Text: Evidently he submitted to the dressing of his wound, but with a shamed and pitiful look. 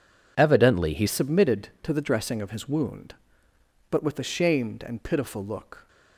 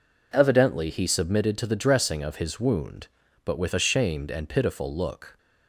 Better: second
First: changes voice at "submitted"; from 1.0 s on; 4.8 s long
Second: none

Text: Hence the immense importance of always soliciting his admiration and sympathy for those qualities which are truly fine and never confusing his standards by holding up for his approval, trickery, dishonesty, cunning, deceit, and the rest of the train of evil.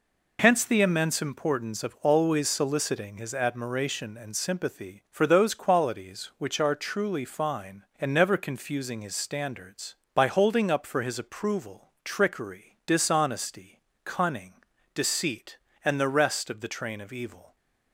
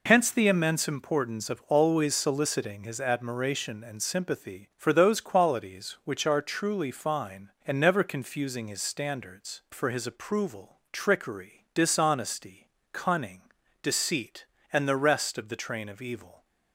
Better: first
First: none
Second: skips "by holding up"; at 9.6 s

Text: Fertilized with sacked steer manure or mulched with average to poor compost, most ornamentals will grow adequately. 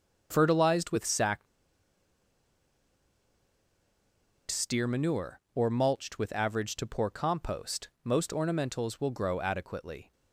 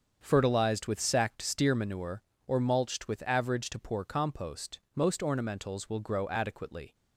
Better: second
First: starts louder than the rest; until 1.3 s; 7 dB // pauses between "sacked" and "steer"; strong; at 1.4 s; 3.0 s long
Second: starts louder than the rest; until 1.2 s; 7 dB

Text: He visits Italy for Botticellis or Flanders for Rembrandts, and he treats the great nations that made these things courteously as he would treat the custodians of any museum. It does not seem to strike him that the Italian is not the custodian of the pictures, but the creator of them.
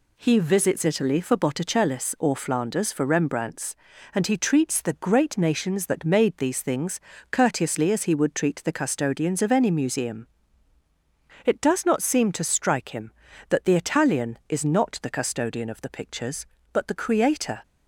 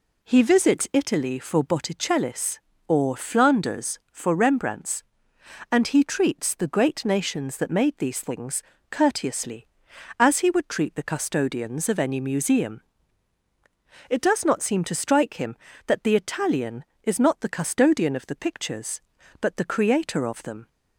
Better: second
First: pauses between "things" and "courteously"; slight; at 6.9 s; 0.32 s long // stops before "of them"; at 17.6 s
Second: pauses between "things" and "courteously"; slight; at 8.6 s; 0.28 s long

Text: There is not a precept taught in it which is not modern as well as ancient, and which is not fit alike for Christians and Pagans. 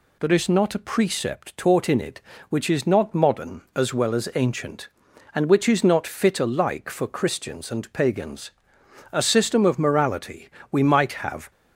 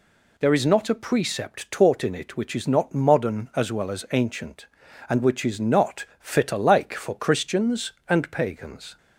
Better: second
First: goes on to say "A system of morality we might have"; strong; from 9.1 s on; 2.3 s long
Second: none

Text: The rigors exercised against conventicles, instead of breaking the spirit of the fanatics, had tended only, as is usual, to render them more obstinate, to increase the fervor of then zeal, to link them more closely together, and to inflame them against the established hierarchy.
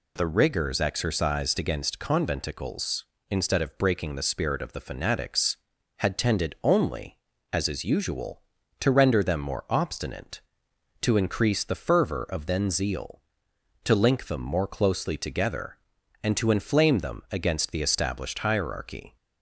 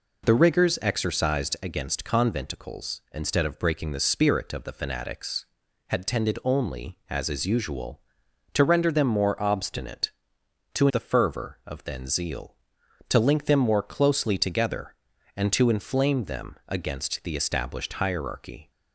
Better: first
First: none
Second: skips "increase"; at 10.8 s

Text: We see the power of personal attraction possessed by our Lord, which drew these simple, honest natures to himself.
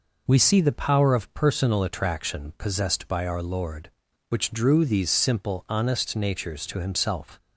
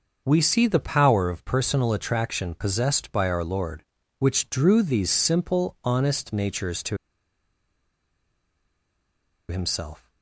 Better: first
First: none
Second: starts louder than the rest; until 1.2 s; 6 dB // pauses between "to" and "himself"; strong; at 6.9 s; 2.5 s long

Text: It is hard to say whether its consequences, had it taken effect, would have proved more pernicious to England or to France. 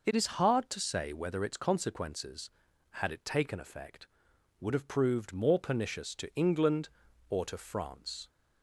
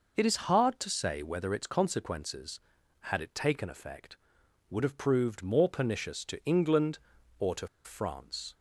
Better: first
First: none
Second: pauses between "to" and "France"; slight; at 7.6 s; 0.17 s long

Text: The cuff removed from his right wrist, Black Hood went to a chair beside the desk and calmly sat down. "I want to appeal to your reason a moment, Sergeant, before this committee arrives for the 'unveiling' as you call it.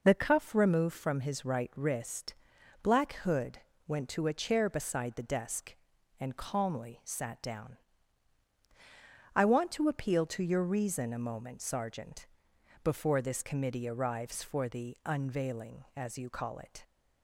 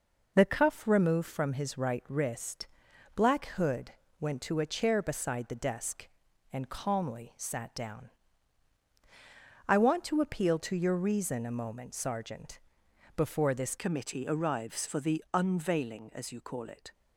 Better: first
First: pauses between "Hood" and "went"; slight; at 3.5 s; 0.28 s long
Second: pauses between "Hood" and "went"; slight; at 3.9 s; 0.28 s long // changes voice at "committee"; from 13.7 s on; 3.2 s long

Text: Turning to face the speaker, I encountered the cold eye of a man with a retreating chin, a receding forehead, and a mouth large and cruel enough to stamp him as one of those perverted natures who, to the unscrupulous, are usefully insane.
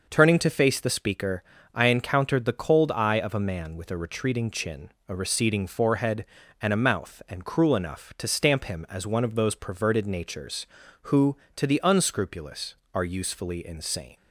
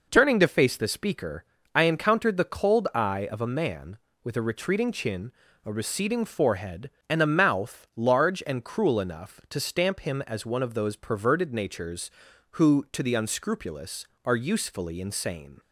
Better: second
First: skips "large"; at 7.2 s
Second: none

